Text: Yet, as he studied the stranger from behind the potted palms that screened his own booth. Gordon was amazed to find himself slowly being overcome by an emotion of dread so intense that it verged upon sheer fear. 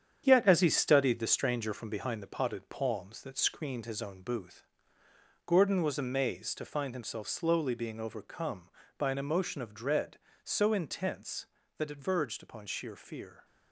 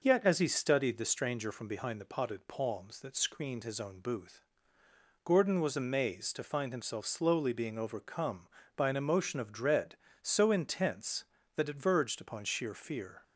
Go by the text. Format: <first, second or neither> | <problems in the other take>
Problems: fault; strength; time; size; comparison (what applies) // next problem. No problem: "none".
second | gets quieter; throughout; 7 dB